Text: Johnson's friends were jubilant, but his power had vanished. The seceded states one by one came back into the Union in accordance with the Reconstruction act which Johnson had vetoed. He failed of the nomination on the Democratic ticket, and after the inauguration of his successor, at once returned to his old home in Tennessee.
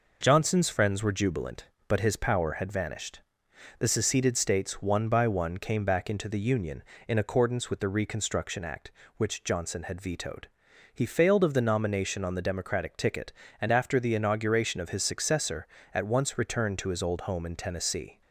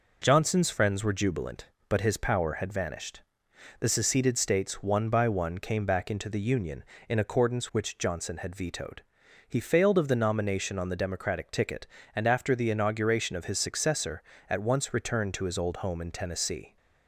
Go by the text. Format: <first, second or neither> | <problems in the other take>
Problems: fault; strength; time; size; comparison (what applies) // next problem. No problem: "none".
first | skips "with the Reconstruction act"; at 7.6 s